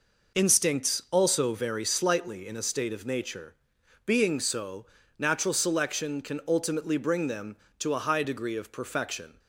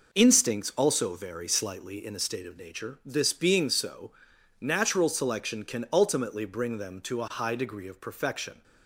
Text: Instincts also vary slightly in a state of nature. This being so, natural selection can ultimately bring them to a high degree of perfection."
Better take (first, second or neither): second